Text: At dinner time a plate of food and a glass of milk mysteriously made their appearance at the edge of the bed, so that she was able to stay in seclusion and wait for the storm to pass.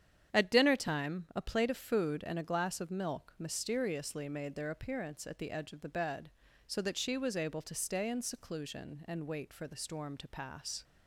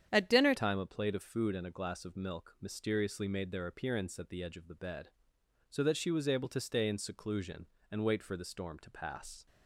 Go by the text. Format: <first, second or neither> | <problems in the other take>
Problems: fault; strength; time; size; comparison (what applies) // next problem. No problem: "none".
first | starts louder than the rest; strong; until 1.1 s; 9 dB; strong in the first // changes voice at "time"; from 0.5 s on; 8.9 s long